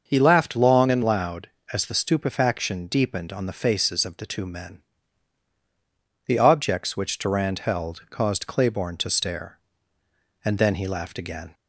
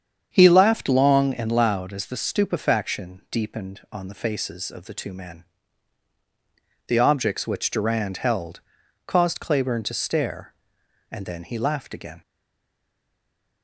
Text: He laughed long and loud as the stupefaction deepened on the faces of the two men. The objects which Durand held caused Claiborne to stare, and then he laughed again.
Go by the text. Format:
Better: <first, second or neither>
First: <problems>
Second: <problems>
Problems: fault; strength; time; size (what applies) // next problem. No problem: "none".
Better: first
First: starts louder than the rest; until 1.0 s; 6 dB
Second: starts louder than the rest; strong; until 1.3 s; 8 dB // pauses between "held" and "caused"; noticeable; at 8.6 s; 0.46 s long // stays silent after the last word; noticeable; from 12.2 s on; 1.4 s long